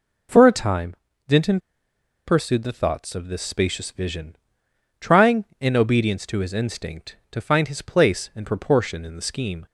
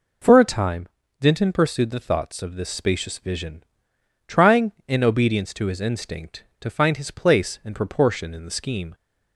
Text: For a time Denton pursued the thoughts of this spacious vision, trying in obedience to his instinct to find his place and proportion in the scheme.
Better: second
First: pauses between "time" and "Denton"; slight; at 0.9 s; 0.32 s long // pauses between "Denton" and "pursued"; noticeable; at 1.5 s; 0.68 s long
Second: pauses between "time" and "Denton"; slight; at 0.8 s; 0.32 s long

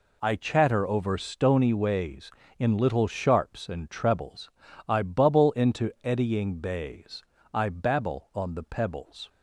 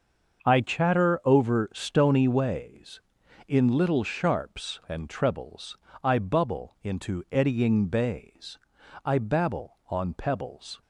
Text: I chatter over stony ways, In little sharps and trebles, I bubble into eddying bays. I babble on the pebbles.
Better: first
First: none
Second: starts louder than the rest; until 1.4 s; 6.5 dB // skips "the"; at 10.1 s

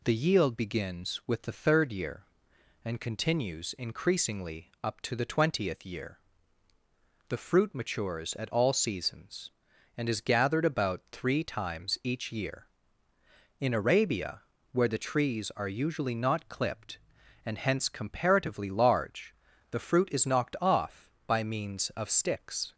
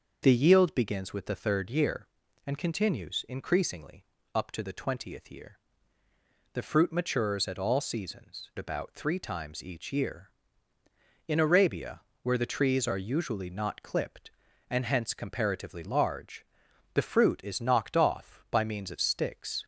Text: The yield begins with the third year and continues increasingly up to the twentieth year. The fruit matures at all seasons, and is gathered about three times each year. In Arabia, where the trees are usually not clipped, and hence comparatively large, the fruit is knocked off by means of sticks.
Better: first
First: none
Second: starts louder than the rest; until 1.2 s; 6.5 dB // pauses between "increasingly" and "up"; slight; at 4.0 s; 0.28 s long // skips "and is gathered"; at 8.5 s

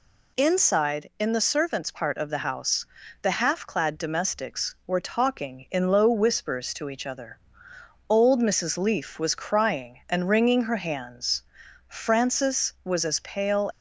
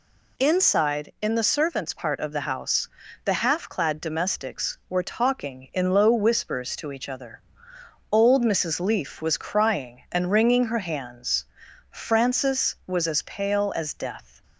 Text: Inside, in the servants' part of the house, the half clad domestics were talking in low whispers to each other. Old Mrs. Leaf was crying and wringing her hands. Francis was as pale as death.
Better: second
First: stops before "as death"; at 13.7 s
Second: none

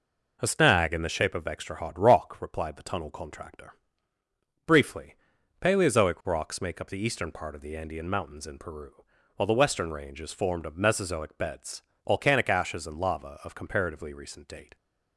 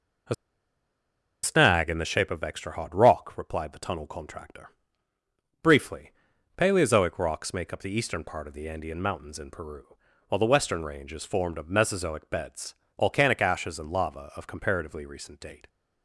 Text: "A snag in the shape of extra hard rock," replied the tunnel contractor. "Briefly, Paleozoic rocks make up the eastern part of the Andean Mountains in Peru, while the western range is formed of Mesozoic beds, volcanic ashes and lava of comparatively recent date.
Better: first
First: none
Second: pauses between "A" and "snag"; at 0.3 s; 1.0 s long

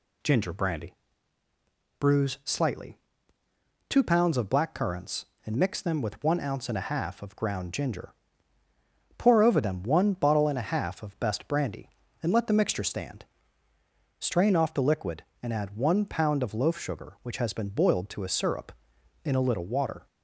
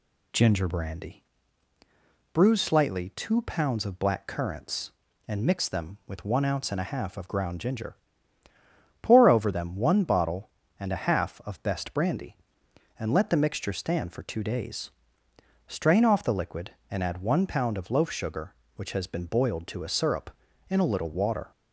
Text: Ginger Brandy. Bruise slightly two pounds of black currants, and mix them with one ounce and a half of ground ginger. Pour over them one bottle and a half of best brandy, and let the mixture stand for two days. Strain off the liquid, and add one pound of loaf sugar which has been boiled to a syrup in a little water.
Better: second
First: pauses between "slightly" and "two"; noticeable; at 2.9 s; 0.92 s long // skips "for two days"; at 13.7 s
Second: none

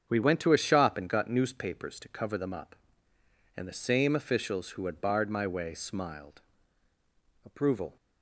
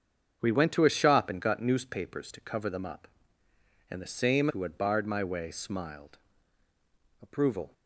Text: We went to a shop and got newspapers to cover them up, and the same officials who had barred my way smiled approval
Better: first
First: starts louder than the rest; strong; until 1.1 s; 7 dB // pauses between "smiled" and "approval"; at 6.4 s; 1.0 s long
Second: starts louder than the rest; strong; until 1.4 s; 7 dB // skips "officials"; at 4.4 s // pauses between "smiled" and "approval"; at 6.1 s; 1.0 s long

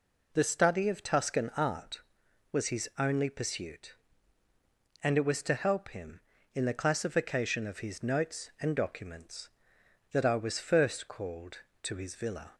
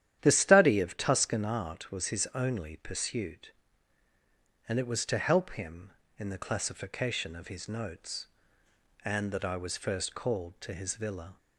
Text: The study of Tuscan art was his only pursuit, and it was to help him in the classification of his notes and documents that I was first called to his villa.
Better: first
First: none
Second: starts louder than the rest; strong; until 1.2 s; 11 dB // skips "documents"; at 9.2 s

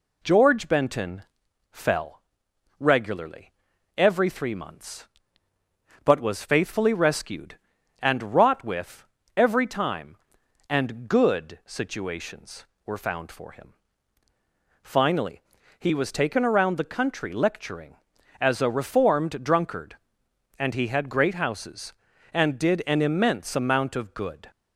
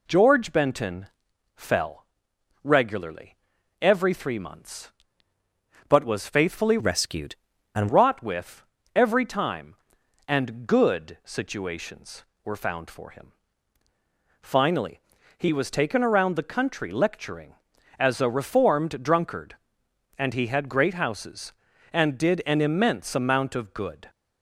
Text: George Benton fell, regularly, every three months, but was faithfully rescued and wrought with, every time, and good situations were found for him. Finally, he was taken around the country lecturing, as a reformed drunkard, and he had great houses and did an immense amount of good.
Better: first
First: pauses between "Benton" and "fell"; noticeable; at 1.2 s; 0.48 s long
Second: pauses between "Benton" and "fell"; noticeable; at 1.0 s; 0.48 s long // changes voice from "rescued" to "and"; from 6.7 to 7.8 s; 1.1 s long

